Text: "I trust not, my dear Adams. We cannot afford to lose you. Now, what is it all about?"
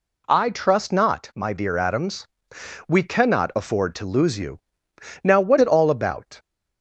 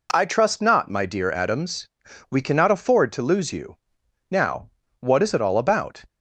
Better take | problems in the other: second | skips "is"; at 5.5 s

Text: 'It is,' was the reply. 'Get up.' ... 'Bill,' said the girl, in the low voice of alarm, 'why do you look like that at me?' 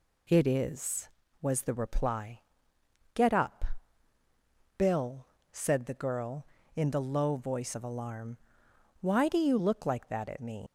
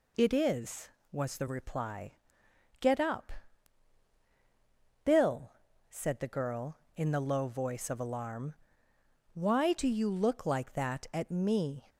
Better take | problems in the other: second | leaves "me" unfinished; at 10.6 s; 135 ms

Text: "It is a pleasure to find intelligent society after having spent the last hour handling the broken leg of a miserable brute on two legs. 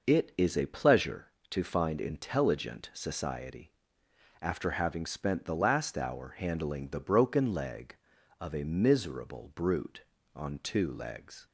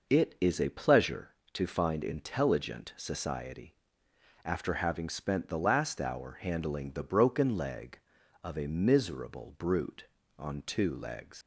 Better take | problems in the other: first | pauses between "society" and "after"; noticeable; at 3.7 s; 0.70 s long; noticeable in the first // leaves "legs" unfinished; at 11.4 s; 80 ms

